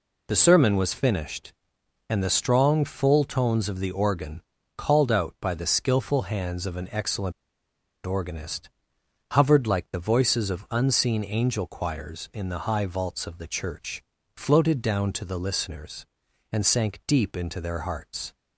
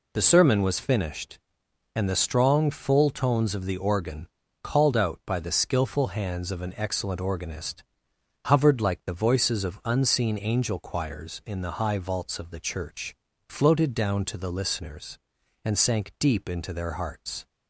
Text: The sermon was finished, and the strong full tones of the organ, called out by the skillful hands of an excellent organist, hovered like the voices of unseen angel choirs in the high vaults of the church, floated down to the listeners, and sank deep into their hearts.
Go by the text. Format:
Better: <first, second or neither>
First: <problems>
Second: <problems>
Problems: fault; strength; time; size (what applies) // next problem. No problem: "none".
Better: second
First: pauses between "excellent" and "organist"; noticeable; at 7.3 s; 0.72 s long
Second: none